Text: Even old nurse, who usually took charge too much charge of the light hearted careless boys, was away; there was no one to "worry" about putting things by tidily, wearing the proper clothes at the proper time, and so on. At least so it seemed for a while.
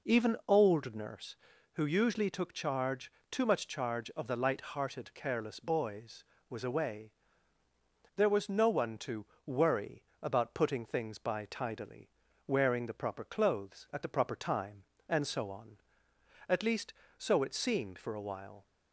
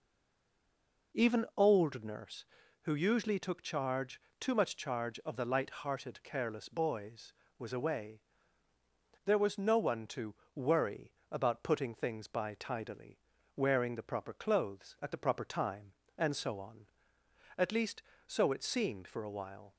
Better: first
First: pauses between "charge" and "too"; slight; at 3.1 s; 0.18 s long // pauses between "to" and "worry"; slight; at 9.2 s; 0.18 s long // pauses between "worry" and "about"; slight; at 10.0 s; 0.22 s long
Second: stays silent before the first word; until 1.1 s; 1.1 s long // pauses between "charge" and "too"; slight; at 4.1 s; 0.18 s long // pauses between "to" and "worry"; slight; at 10.3 s; 0.18 s long // pauses between "worry" and "about"; slight; at 11.0 s; 0.22 s long

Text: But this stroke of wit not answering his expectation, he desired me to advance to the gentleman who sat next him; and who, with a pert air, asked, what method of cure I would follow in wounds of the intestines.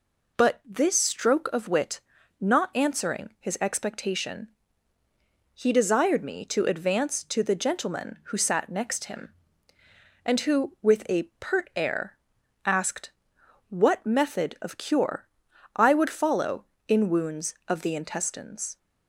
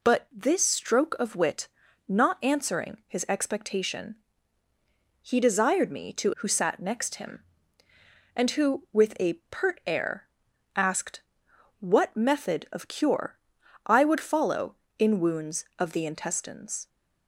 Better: first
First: pauses between "wit" and "not"; at 1.9 s; 0.40 s long // pauses between "a" and "pert"; slight; at 11.2 s; 0.18 s long // pauses between "cure" and "I"; noticeable; at 15.2 s; 0.48 s long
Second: pauses between "wit" and "not"; at 1.6 s; 0.40 s long // skips "advance to the gentleman"; at 6.3 s // pauses between "a" and "pert"; slight; at 9.3 s; 0.18 s long // pauses between "cure" and "I"; noticeable; at 13.3 s; 0.48 s long

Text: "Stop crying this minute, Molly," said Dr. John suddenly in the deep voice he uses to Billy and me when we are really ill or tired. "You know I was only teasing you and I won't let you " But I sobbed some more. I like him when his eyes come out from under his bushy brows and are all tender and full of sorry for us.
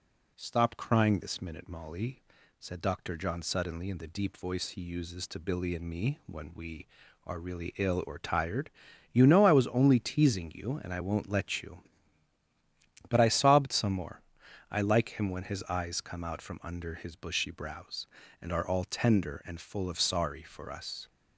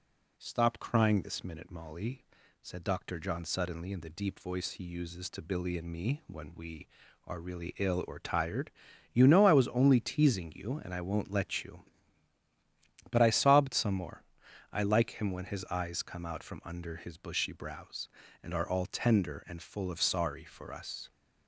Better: neither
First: none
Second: none

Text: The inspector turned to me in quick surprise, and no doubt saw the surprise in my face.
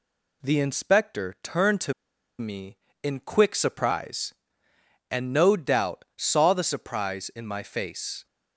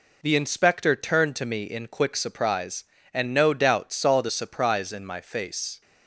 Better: second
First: pauses between "to" and "me"; noticeable; at 1.9 s; 0.46 s long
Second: none

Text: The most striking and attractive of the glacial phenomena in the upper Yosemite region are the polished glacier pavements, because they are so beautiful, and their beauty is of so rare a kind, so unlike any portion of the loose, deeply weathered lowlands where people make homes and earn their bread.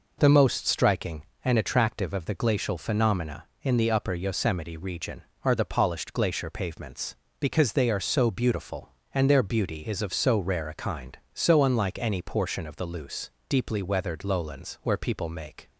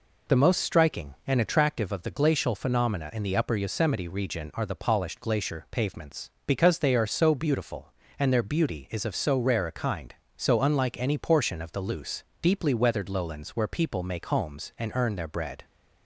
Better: second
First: stops before "homes and earn their bread"; at 15.6 s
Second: none

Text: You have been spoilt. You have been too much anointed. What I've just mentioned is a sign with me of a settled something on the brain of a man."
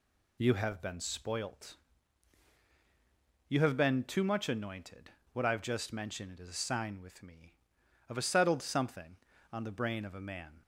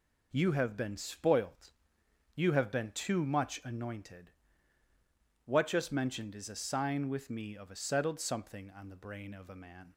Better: first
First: none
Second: skips "I've"; at 5.6 s

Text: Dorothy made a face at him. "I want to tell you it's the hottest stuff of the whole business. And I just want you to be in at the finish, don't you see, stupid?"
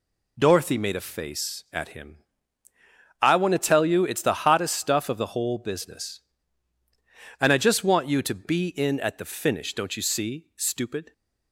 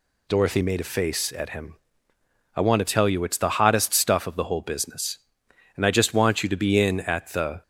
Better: first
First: none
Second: stops before "finish don't you see stupid"; at 7.6 s

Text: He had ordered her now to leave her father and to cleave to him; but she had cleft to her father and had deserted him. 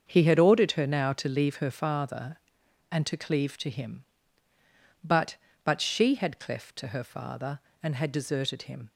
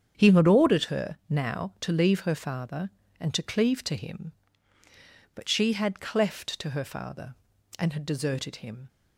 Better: second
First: starts louder than the rest; until 1.0 s; 7 dB // says "but" twice; at 5.6 s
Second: starts louder than the rest; strong; until 1.1 s; 8 dB

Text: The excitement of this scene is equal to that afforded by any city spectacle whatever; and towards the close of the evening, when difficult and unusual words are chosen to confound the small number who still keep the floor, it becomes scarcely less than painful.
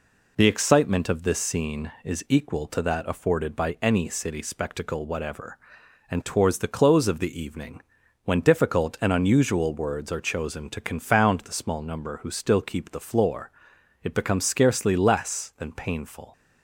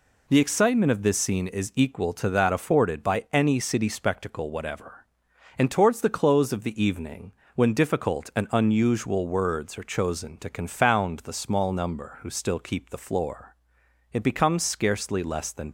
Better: first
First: none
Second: stops before "painful"; at 15.6 s

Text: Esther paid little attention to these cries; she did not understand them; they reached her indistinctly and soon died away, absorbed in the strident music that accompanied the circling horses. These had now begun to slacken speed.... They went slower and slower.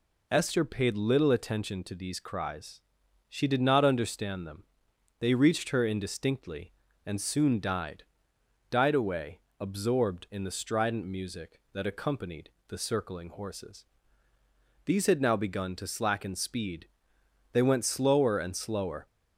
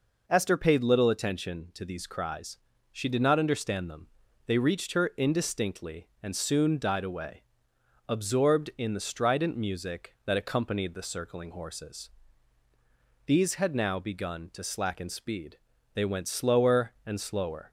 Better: second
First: says "died" twice; at 8.6 s // pauses between "accompanied" and "the"; slight; at 12.4 s; 0.18 s long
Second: none

